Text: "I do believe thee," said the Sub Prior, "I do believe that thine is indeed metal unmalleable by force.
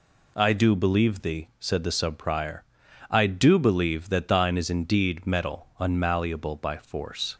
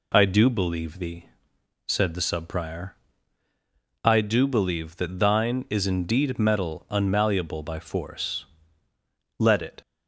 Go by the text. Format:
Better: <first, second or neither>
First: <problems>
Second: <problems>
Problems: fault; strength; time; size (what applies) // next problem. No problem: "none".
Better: first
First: none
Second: goes on to say "Let it"; slight; from 9.3 s on; 0.42 s long